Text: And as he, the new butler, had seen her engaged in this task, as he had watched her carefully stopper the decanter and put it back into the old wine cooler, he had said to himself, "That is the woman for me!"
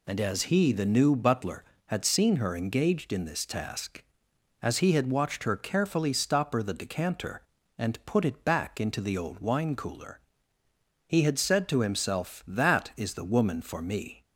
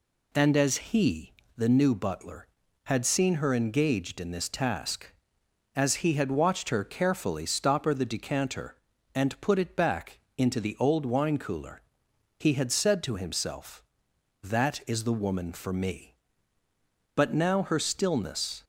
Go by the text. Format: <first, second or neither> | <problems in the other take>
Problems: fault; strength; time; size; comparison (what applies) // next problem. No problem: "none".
first | pauses between "back" and "into"; slight; at 10.1 s; 0.18 s long // goes on to say "But now her stillness"; from 17.1 s on; 1.4 s long